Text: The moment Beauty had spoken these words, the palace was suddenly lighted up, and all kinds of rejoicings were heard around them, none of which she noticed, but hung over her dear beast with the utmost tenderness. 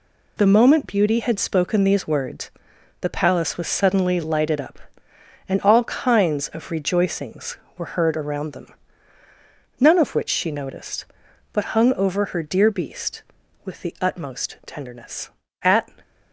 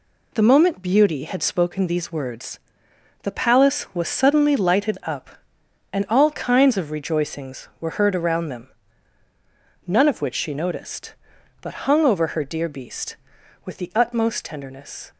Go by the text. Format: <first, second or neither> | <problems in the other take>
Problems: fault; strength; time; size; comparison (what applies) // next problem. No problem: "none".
second | goes on to say "At"; slight; from 15.6 s on; 0.26 s long